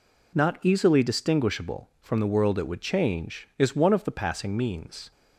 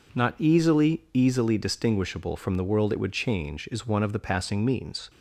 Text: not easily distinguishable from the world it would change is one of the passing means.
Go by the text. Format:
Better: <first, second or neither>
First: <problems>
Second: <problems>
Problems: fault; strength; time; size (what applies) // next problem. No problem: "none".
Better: first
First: none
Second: says "easily" twice; at 1.1 s